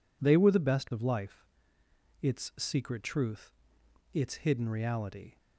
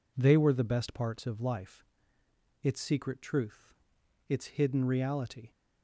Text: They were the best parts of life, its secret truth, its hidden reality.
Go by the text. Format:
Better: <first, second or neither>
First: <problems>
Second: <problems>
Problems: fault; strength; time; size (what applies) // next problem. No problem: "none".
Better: second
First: skips "parts"; at 0.9 s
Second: none